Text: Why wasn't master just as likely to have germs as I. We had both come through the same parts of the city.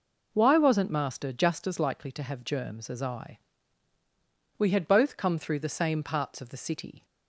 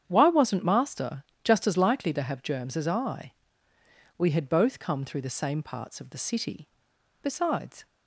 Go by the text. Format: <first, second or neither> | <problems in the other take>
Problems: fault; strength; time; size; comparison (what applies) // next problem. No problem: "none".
first | starts louder than the rest; strong; until 1.0 s; 8.5 dB // pauses between "master" and "just"; slight; at 1.2 s; 0.20 s long // goes on to say "Besides"; noticeable; from 7.2 s on; 0.64 s long